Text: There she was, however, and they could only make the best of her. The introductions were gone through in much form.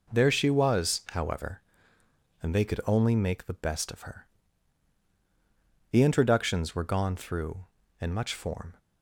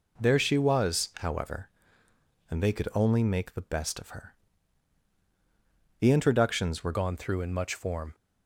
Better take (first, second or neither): first